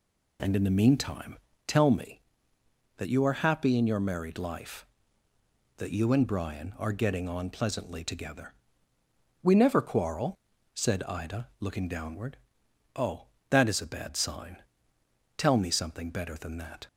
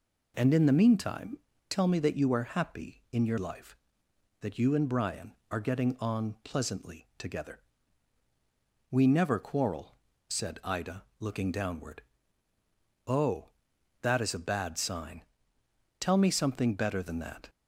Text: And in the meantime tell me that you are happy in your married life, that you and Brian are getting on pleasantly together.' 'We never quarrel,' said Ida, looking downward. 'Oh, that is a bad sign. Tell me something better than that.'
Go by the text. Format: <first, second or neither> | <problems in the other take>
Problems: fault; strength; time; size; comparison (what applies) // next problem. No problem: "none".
first | pauses between "meantime" and "tell"; slight; at 1.3 s; 0.30 s long; slight in the first // skips "married"; at 3.3 s